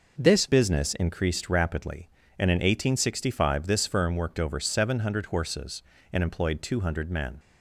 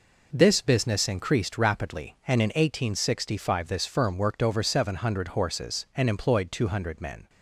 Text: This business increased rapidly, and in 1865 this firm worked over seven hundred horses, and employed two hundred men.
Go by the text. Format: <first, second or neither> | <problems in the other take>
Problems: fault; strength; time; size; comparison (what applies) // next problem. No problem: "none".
second | changes voice at "business"; from 0.4 s on; 6.9 s long